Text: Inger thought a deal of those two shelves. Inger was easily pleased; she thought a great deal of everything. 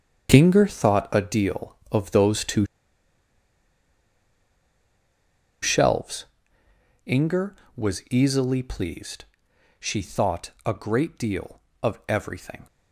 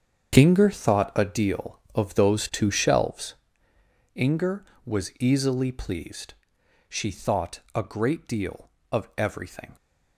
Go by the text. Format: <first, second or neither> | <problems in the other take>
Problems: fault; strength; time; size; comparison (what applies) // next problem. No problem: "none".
second | starts louder than the rest; strong; until 1.3 s; 7.5 dB; strong in the second // pauses between "two" and "shelves"; strong; at 2.6 s; 2.9 s long